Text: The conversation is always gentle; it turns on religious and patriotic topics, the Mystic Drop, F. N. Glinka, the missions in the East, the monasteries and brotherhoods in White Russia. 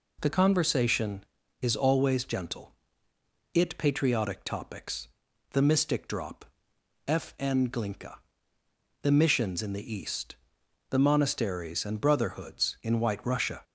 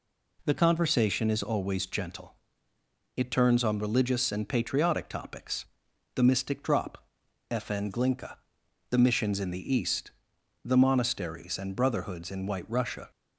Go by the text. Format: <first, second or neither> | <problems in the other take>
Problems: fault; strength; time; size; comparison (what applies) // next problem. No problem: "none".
second | skips "turns on religious and"; at 3.7 s